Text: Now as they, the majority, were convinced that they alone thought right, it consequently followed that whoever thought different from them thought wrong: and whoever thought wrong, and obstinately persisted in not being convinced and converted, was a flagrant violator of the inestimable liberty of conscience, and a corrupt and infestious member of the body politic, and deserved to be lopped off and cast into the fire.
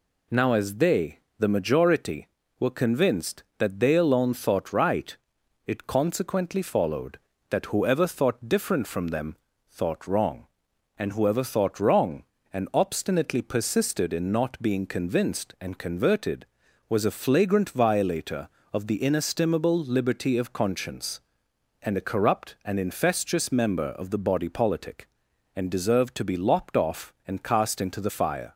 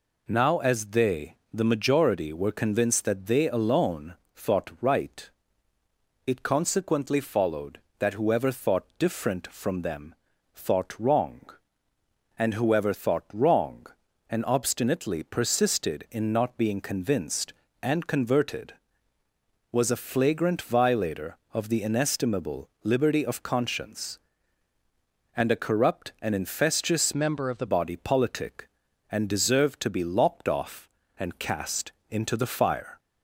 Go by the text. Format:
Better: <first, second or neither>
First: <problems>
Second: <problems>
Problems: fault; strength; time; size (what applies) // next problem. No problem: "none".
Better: first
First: pauses between "them" and "thought"; slight; at 9.3 s; 0.32 s long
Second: pauses between "alone" and "thought"; slight; at 4.1 s; 0.22 s long // pauses between "them" and "thought"; at 10.1 s; 0.40 s long // pauses between "inestimable" and "liberty"; slight; at 22.6 s; 0.16 s long // changes voice from "member" to "the"; from 27.1 to 27.6 s; 0.5 s long // pauses between "cast" and "into"; slight; at 31.9 s; 0.18 s long